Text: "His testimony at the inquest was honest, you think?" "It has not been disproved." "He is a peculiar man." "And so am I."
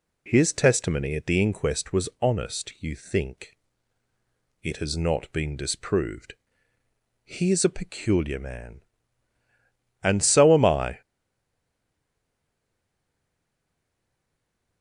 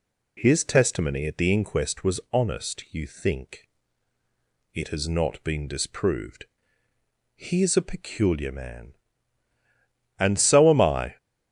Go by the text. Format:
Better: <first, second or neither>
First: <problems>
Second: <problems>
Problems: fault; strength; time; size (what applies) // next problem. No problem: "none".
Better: second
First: stays silent after the last word; strong; from 11.0 s on; 3.8 s long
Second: none